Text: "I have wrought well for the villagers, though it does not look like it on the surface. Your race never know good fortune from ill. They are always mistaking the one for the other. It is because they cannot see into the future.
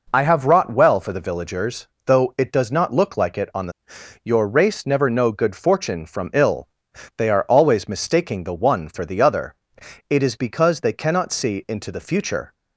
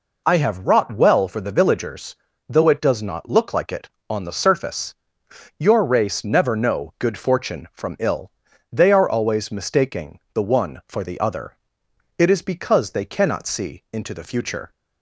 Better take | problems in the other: second | skips "surface"; at 3.9 s

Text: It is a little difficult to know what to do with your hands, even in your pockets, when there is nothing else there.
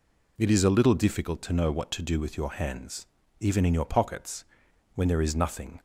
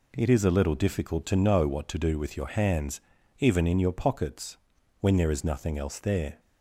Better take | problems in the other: second | stops before "else there"; at 5.7 s

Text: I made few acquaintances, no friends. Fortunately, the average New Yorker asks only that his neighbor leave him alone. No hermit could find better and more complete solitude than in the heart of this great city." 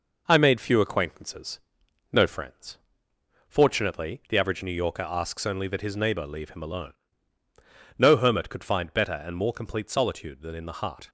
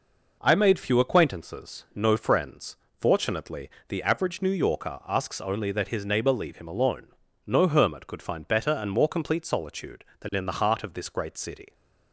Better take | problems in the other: second | stops before "of this great city"; at 11.0 s

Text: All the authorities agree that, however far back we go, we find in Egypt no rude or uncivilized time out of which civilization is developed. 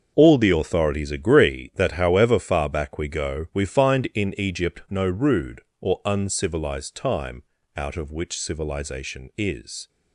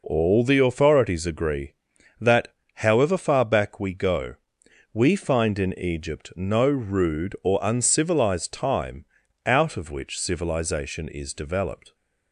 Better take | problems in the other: second | starts louder than the rest; until 1.1 s; 6.5 dB // pauses between "time" and "out"; slight; at 7.4 s; 0.34 s long; also in the second // stops before "developed"; at 9.8 s

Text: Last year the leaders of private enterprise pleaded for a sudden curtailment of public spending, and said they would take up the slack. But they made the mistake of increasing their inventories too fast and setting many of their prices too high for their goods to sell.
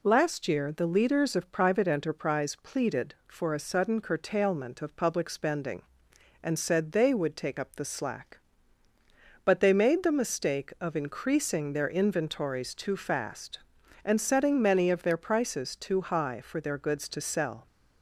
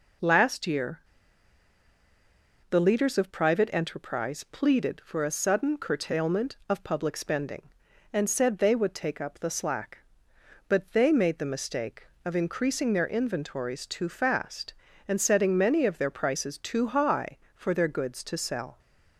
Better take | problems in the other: first | pauses between "year" and "the"; strong; at 0.9 s; 1.7 s long

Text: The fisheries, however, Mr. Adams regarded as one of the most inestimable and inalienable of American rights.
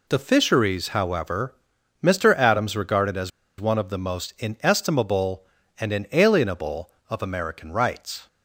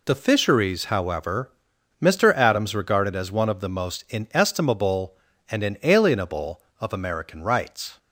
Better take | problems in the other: second | pauses between "as" and "one"; slight; at 3.3 s; 0.30 s long

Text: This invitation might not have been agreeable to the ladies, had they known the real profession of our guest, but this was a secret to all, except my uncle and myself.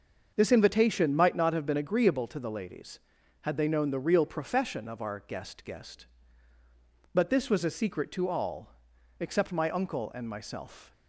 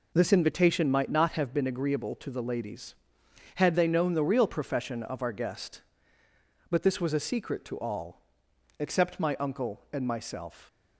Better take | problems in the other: second | starts louder than the rest; until 1.3 s; 6.5 dB // says "guest" twice; at 5.6 s

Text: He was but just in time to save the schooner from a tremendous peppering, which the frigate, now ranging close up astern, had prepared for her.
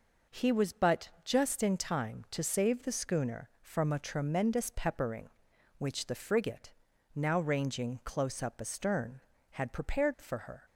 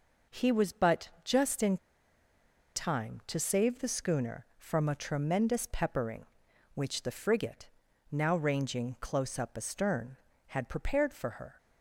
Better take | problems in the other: first | pauses between "but" and "just"; slight; at 1.0 s; 0.16 s long; slight in the first // pauses between "in" and "time"; at 1.7 s; 0.99 s long

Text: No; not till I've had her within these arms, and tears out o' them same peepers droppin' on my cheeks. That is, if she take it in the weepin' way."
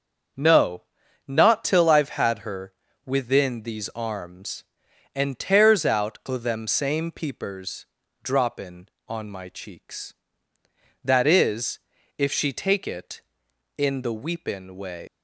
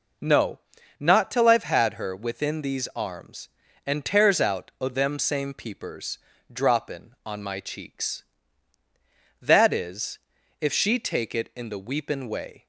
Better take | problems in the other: second | starts louder than the rest; until 1.8 s; 6.5 dB // pauses between "her" and "within"; slight; at 2.7 s; 0.32 s long // pauses between "peepers" and "droppin"; slight; at 7.8 s; 0.36 s long; slight in the second // leaves "way" unfinished; at 15.0 s; 170 ms

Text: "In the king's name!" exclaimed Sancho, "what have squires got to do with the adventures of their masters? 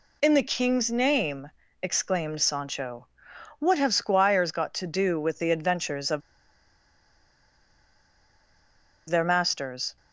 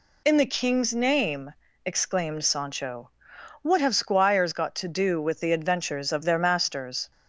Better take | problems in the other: second | pauses between "of" and "their"; strong; at 6.2 s; 2.8 s long

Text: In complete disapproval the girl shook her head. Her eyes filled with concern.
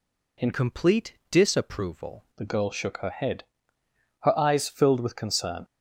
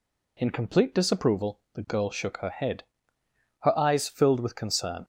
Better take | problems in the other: second | changes voice from "complete" to "disapproval"; from 0.5 to 2.2 s; 1.7 s long // pauses between "complete" and "disapproval"; slight; at 1.1 s; 0.16 s long

